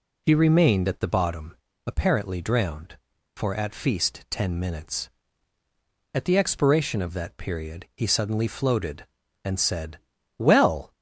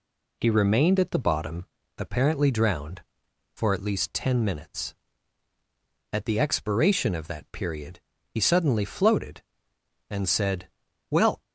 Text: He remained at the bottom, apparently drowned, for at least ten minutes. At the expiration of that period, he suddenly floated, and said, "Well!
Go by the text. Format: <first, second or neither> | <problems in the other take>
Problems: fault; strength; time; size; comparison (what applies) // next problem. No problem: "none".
second | says "feast" for "least"; at 3.7 s